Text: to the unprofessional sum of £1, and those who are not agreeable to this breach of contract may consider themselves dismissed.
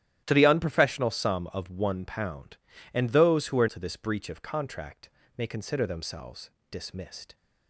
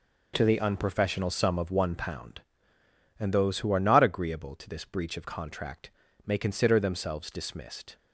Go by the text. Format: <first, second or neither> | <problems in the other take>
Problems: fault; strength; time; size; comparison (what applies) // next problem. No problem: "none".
second | starts louder than the rest; strong; until 1.2 s; 13 dB // skips "not agreeable"; at 3.6 s // pauses between "contract" and "may"; slight; at 5.0 s; 0.28 s long; slight in the second // pauses between "themselves" and "dismissed"; slight; at 6.4 s; 0.20 s long